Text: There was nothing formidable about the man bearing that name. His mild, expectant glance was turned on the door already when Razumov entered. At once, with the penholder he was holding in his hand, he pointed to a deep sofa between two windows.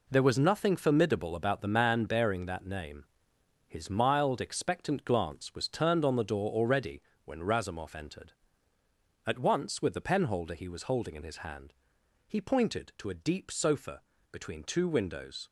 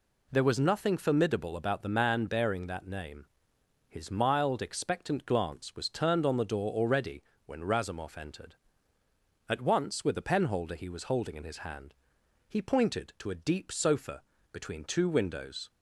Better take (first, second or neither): second